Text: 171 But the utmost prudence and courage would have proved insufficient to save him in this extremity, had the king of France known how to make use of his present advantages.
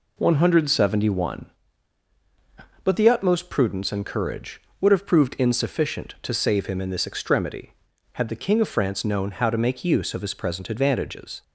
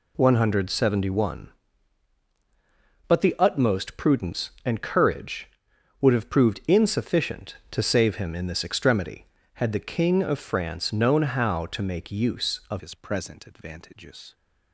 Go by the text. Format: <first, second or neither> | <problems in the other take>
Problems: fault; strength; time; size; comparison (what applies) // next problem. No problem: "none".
first | changes voice at "his"; from 12.7 s on; 1.6 s long